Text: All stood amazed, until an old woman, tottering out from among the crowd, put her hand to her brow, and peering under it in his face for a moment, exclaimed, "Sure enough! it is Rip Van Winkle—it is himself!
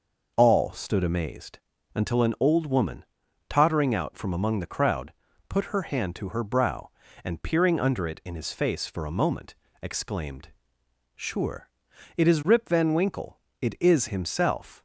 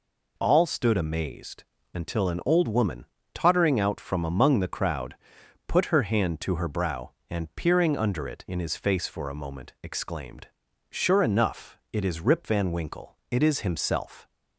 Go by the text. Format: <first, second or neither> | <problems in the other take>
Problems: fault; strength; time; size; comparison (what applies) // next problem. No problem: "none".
second | skips "enough"; at 11.9 s